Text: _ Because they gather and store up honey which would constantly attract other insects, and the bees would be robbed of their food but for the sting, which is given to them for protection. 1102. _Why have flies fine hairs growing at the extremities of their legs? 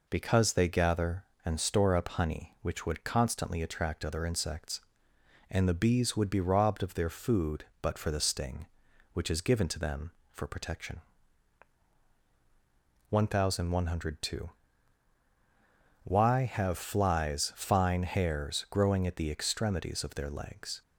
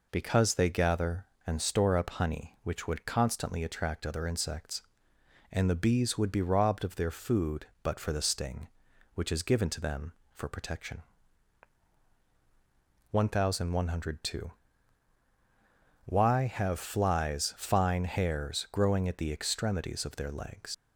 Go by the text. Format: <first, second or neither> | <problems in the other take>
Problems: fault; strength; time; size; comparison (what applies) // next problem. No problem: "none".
first | leaves "legs" unfinished; at 20.7 s; 80 ms